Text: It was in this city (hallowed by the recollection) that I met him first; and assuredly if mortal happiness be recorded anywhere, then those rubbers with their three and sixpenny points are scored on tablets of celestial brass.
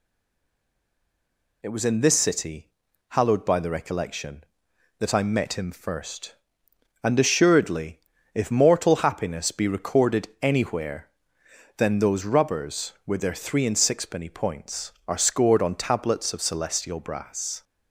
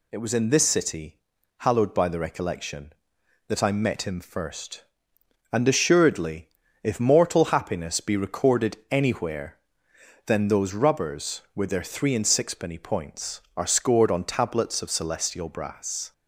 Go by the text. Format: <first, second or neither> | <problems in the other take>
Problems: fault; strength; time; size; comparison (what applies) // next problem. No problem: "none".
second | stays silent before the first word; noticeable; until 1.6 s; 1.6 s long // pauses between "assuredly" and "if"; at 7.9 s; 0.38 s long; also in the second